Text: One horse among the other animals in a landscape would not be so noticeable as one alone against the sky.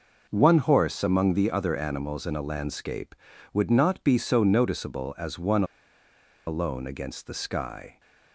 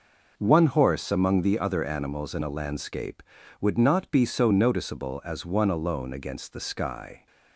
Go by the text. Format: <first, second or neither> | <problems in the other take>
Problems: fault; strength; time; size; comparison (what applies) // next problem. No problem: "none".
second | pauses between "one" and "alone"; noticeable; at 5.6 s; 0.83 s long